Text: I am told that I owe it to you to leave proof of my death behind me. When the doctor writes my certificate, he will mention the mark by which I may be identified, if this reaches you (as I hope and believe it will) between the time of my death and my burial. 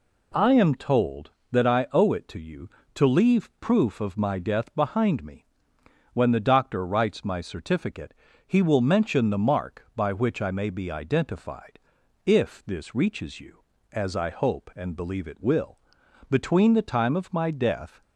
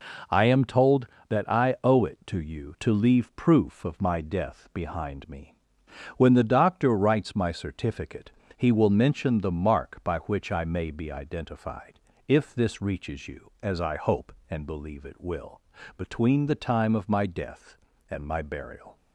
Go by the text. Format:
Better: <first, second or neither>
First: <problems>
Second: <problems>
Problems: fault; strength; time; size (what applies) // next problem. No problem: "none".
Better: second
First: stops before "and my burial"; at 18.0 s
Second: none